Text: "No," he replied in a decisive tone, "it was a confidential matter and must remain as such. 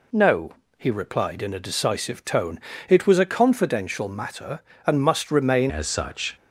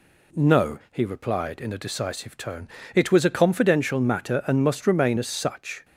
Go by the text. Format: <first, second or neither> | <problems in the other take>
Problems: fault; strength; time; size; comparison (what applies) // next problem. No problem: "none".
second | changes voice at "as"; from 5.6 s on; 0.7 s long